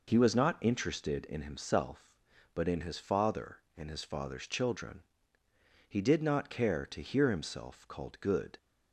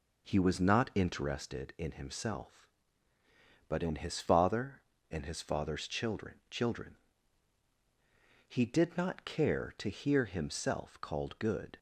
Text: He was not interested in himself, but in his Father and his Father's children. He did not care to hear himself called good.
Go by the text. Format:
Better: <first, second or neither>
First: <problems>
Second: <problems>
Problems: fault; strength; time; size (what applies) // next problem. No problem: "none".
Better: first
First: none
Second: says "children" twice; at 6.4 s